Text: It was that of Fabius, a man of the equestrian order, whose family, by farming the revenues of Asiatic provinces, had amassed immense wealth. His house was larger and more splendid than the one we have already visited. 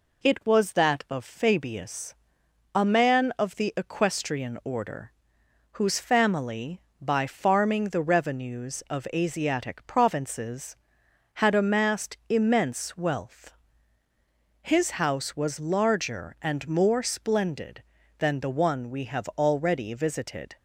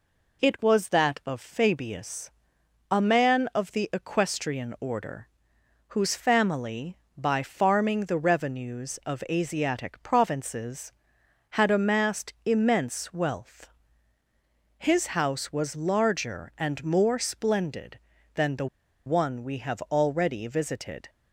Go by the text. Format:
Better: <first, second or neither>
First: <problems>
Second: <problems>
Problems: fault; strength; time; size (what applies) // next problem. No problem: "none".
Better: first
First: none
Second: pauses between "the" and "one"; at 18.6 s; 0.40 s long